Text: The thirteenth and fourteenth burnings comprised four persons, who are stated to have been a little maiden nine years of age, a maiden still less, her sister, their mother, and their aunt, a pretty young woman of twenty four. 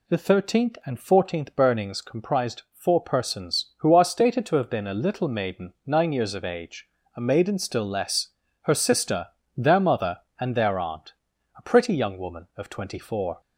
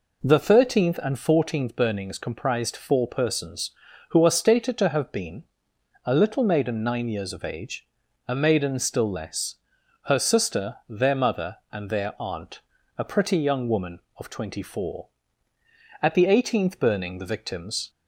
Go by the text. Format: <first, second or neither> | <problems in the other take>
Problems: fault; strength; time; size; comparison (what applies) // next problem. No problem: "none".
first | pauses between "been" and "a"; noticeable; at 5.4 s; 0.62 s long // goes on to say "At the eighteenth burning the victims"; strong; from 16.0 s on; 1.8 s long